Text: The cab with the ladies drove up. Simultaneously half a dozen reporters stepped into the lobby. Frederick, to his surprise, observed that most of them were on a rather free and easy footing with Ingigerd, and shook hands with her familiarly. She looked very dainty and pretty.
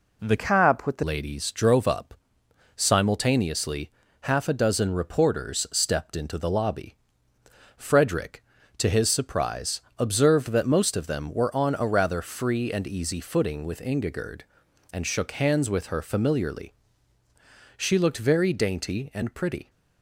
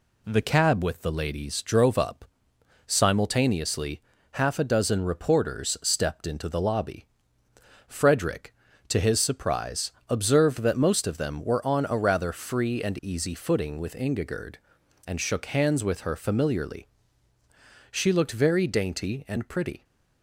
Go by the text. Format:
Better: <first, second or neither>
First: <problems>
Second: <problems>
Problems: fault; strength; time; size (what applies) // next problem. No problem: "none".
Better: second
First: changes voice from "cab" to "the"; from 0.3 to 1.0 s; 0.7 s long // pauses between "Simultaneously" and "half"; slight; at 3.8 s; 0.32 s long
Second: pauses between "Simultaneously" and "half"; slight; at 4.0 s; 0.32 s long